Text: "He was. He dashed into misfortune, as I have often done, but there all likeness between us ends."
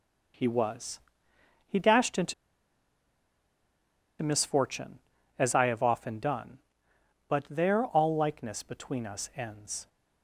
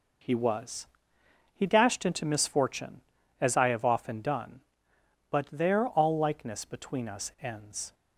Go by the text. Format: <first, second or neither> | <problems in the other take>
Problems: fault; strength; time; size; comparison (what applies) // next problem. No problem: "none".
second | pauses between "into" and "misfortune"; strong; at 2.3 s; 1.8 s long